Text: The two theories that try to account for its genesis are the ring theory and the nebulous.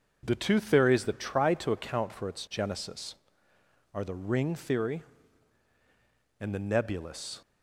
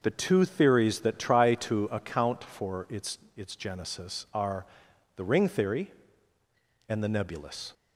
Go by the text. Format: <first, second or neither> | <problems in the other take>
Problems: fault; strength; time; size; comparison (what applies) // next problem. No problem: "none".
first | starts louder than the rest; noticeable; until 1.0 s; 6 dB // says "its" twice; at 3.3 s // pauses between "are" and "the"; noticeable; at 4.6 s; 0.50 s long